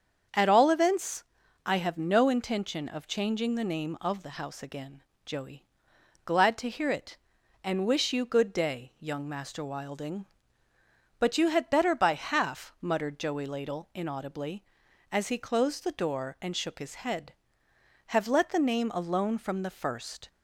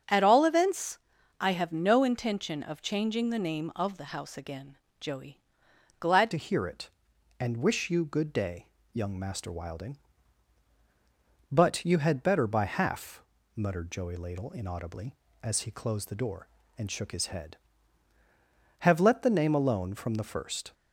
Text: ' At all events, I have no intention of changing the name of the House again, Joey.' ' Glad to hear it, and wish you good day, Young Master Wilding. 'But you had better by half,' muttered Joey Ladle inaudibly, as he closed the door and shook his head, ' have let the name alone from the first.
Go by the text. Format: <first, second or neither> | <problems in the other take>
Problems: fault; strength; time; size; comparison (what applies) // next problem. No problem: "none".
first | starts louder than the rest; strong; until 1.4 s; 8.5 dB; strong in the first // changes voice at "to"; from 6.3 s on; 14.4 s long